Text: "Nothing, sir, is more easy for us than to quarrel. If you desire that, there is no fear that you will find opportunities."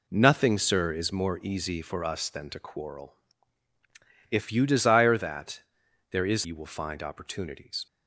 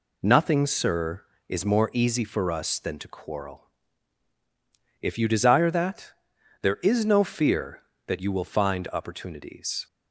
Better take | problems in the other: second | skips "no fear that"; at 6.4 s

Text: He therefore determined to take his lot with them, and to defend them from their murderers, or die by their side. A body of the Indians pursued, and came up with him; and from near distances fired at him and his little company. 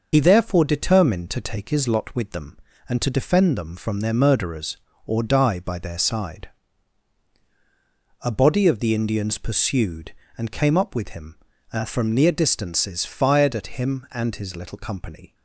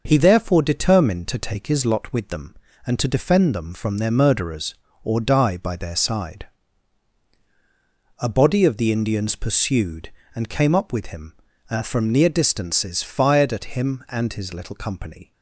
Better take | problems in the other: second | loses the start of "He"; at 0.1 s; 55 ms // starts louder than the rest; noticeable; until 1.1 s; 6 dB; also in the second

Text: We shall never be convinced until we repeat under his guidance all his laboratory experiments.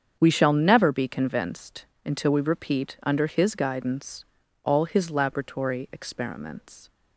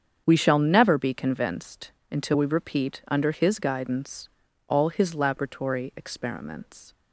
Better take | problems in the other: neither | starts louder than the rest; strong; the same in both // pauses between "convinced" and "until"; slight; the same in both // pauses between "guidance" and "all"; the same in both

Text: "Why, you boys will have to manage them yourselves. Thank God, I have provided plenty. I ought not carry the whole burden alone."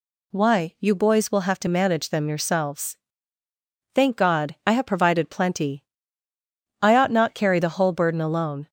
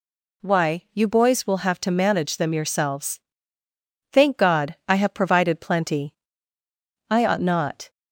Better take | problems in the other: first | stops before "carry the whole burden alone"; at 7.8 s

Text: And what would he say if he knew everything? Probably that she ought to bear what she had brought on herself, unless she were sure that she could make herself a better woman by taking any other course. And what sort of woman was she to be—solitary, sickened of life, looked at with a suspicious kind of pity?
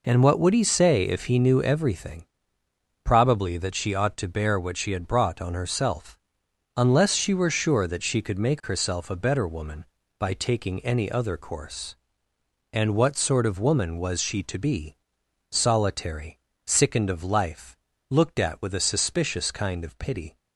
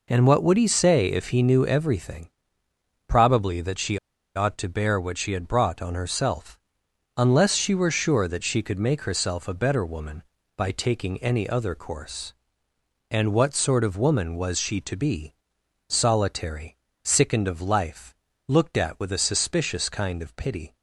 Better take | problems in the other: first | pauses between "she" and "ought"; at 3.9 s; 0.37 s long

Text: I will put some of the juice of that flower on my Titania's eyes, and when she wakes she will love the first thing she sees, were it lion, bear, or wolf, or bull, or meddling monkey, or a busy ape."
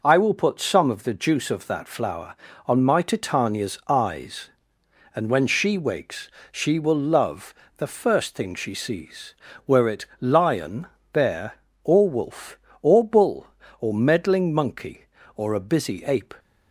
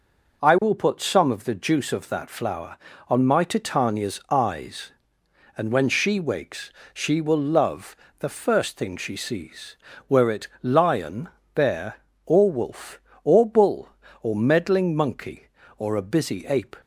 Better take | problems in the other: neither | pauses between "wakes" and "she"; slight; the same in both // pauses between "love" and "the"; slight; the same in both // pauses between "it" and "lion"; slight; the same in both

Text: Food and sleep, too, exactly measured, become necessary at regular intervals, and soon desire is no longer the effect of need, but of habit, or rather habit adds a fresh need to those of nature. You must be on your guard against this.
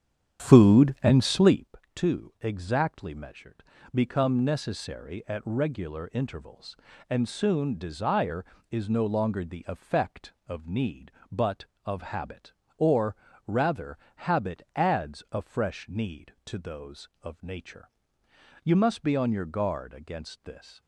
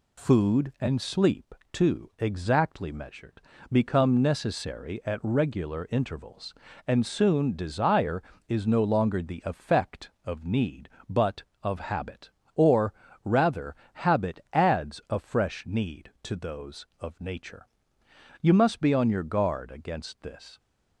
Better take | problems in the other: second | starts louder than the rest; strong; until 1.7 s; 9 dB // pauses between "or" and "rather"; slight; at 13.1 s; 0.32 s long; slight in the second // pauses between "rather" and "habit"; slight; at 13.9 s; 0.18 s long; slight in the second

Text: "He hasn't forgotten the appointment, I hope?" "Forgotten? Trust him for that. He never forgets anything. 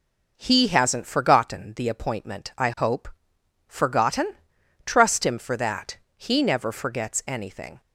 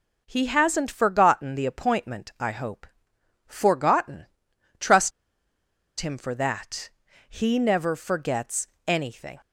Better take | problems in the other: first | pauses between "Trust" and "him"; noticeable; at 5.1 s; 0.89 s long // pauses between "forgets" and "anything"; slight; at 8.6 s; 0.18 s long

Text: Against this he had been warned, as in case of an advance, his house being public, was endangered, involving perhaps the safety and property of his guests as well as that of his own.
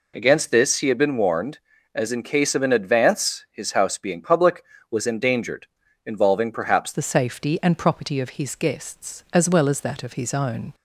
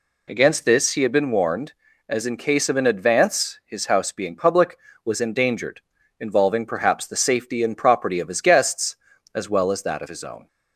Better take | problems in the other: second | changes voice at "the"; from 6.9 s on; 3.8 s long

